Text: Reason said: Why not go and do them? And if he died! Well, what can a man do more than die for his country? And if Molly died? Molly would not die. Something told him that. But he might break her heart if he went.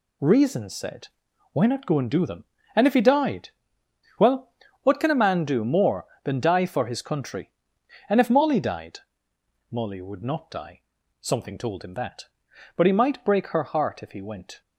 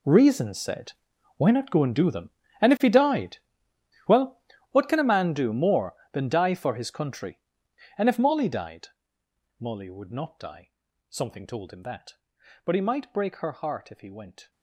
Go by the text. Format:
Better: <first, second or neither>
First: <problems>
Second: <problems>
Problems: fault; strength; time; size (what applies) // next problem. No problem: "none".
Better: first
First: none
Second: gets quieter; strong; throughout; 16 dB